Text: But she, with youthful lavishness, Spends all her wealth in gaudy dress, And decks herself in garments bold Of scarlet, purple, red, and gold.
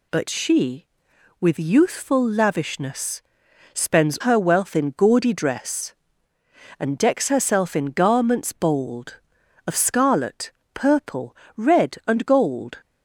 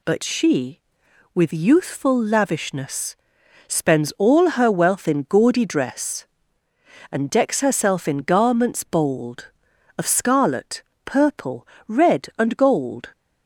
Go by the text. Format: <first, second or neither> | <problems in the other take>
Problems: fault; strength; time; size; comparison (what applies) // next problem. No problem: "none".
second | skips "all"; at 4.1 s